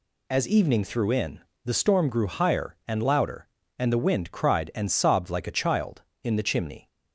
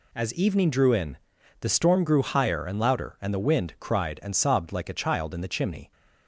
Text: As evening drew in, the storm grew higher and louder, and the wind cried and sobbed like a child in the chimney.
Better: second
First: says "threw" for "drew"; at 0.8 s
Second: none

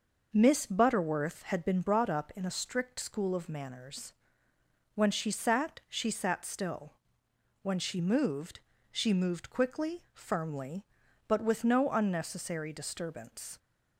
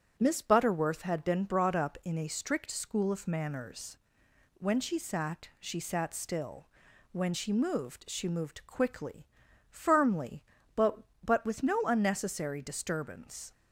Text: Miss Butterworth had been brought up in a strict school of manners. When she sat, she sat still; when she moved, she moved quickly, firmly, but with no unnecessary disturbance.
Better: first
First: none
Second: starts louder than the rest; strong; until 1.1 s; 8.5 dB // says "but" twice; at 11.2 s

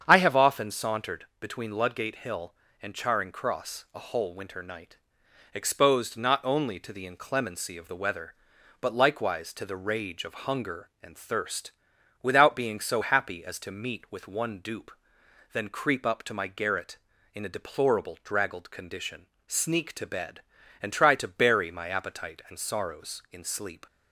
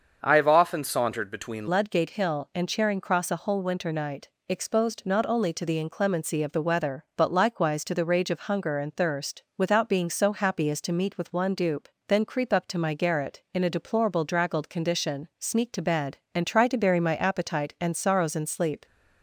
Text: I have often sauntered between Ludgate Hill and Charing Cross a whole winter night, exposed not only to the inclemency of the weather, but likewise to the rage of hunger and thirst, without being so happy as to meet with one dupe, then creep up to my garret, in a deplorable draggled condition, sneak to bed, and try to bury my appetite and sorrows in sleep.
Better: first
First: starts louder than the rest; strong; until 1.0 s; 8 dB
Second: starts louder than the rest; until 1.2 s; 6.5 dB // changes voice at "Ludgate"; from 1.6 s on; 17.2 s long

